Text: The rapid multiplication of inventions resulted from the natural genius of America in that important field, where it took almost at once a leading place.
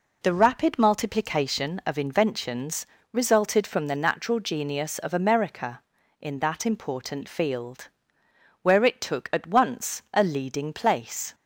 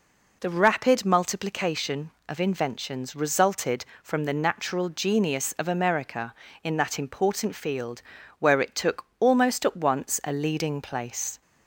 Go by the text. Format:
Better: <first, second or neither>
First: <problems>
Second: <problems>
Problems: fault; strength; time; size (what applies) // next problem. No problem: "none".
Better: second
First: pauses between "inventions" and "resulted"; slight; at 2.8 s; 0.24 s long // skips "almost"; at 9.3 s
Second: none